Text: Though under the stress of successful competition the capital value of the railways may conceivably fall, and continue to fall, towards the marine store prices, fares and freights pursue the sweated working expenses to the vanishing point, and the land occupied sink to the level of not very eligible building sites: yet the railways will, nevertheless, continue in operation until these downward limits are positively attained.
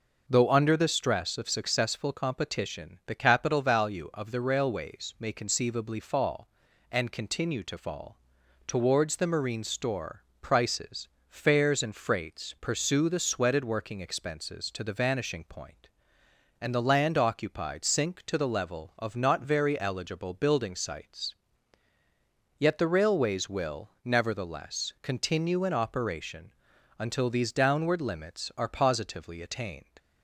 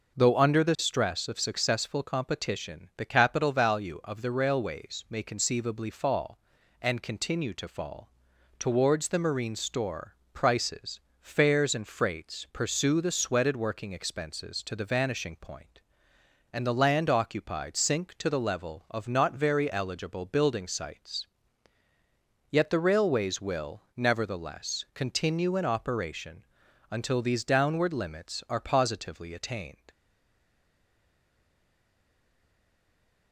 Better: first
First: pauses between "store" and "prices"; slight; at 10.2 s; 0.18 s long // pauses between "operation" and "until"; noticeable; at 26.5 s; 0.46 s long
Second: pauses between "store" and "prices"; slight; at 10.1 s; 0.18 s long // pauses between "operation" and "until"; noticeable; at 26.4 s; 0.46 s long // stays silent after the last word; strong; from 29.9 s on; 3.4 s long

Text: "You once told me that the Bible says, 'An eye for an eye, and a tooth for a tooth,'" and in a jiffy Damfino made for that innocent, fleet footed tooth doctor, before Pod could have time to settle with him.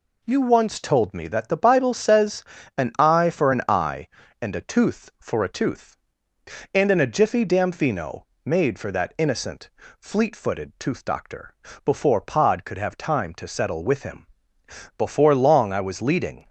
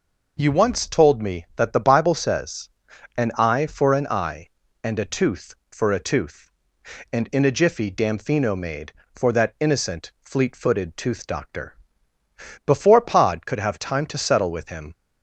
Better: second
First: pauses between "Damfino" and "made"; slight; at 8.2 s; 0.18 s long // goes on to say "Before long I was leading"; from 14.9 s on; 1.5 s long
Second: none

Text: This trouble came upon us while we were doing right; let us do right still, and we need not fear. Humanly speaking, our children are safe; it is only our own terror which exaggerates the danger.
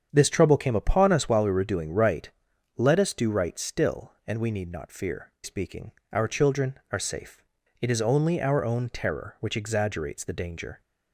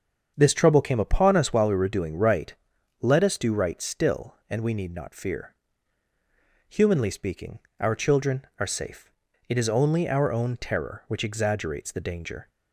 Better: second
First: starts louder than the rest; strong; until 1.1 s; 8 dB // skips "Humanly"; at 5.3 s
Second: starts louder than the rest; until 1.3 s; 7 dB

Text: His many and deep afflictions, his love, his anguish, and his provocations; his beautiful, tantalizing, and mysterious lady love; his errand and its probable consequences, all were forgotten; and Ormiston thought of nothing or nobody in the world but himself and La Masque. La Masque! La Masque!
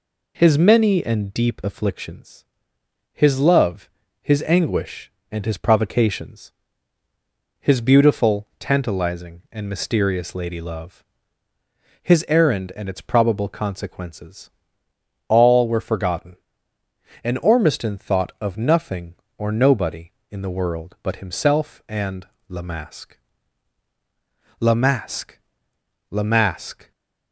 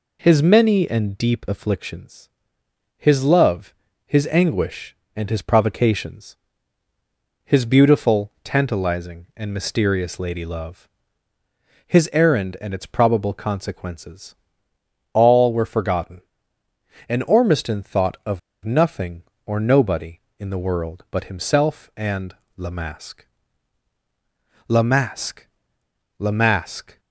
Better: first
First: pauses between "and" and "La"; slight; at 22.2 s; 0.22 s long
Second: pauses between "of" and "nothing"; slight; at 18.3 s; 0.25 s long // pauses between "and" and "La"; slight; at 22.3 s; 0.22 s long

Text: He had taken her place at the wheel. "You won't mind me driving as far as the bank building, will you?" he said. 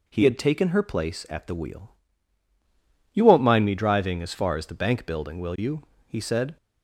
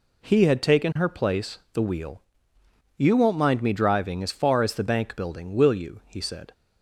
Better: first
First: none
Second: skips "at"; at 1.6 s

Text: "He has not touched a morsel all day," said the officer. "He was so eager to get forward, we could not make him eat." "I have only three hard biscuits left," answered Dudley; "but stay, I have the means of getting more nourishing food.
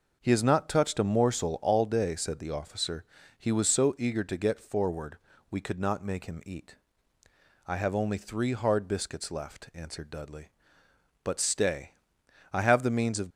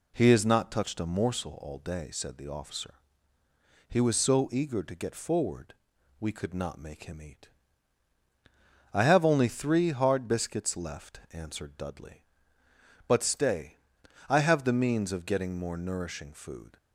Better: second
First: stops before "getting more nourishing food"; at 13.2 s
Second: none

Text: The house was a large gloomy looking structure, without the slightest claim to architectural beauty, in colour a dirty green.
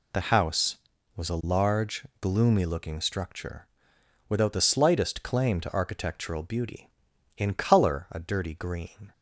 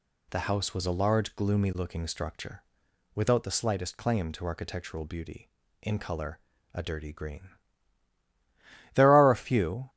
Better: first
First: none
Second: pauses between "colour" and "a"; slight; at 6.3 s; 0.32 s long // goes on to say "There are a few"; noticeable; from 8.9 s on; 0.96 s long

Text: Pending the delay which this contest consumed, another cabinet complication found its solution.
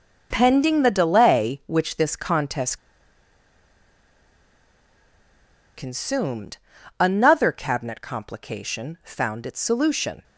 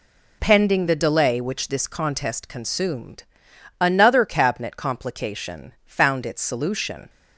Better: second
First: pauses between "contest" and "consumed"; strong; at 2.7 s; 2.9 s long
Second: none

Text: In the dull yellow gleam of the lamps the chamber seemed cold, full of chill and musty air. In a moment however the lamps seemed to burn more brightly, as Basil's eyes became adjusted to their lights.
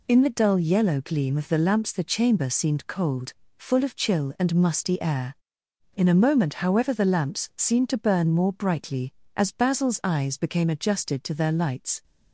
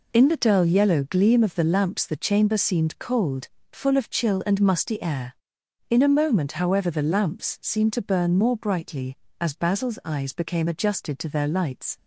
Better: neither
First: none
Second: none

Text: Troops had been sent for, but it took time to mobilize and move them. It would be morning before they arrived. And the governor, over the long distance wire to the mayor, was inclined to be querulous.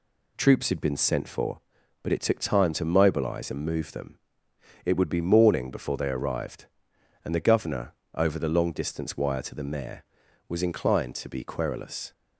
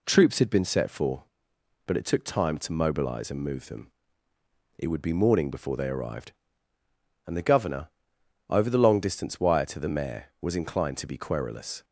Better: first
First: none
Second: says "set" for "sent"; at 0.6 s

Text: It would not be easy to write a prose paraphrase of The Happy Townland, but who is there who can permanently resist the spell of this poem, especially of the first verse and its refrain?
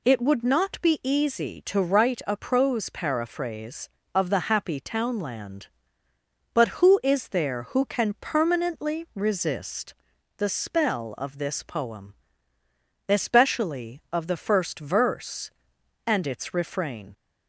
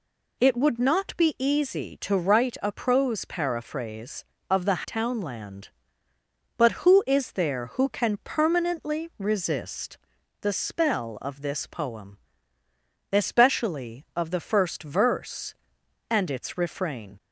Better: first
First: pauses between "resist" and "the"; noticeable; at 9.9 s; 0.46 s long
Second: skips "Happy"; at 4.8 s // pauses between "resist" and "the"; noticeable; at 9.9 s; 0.46 s long

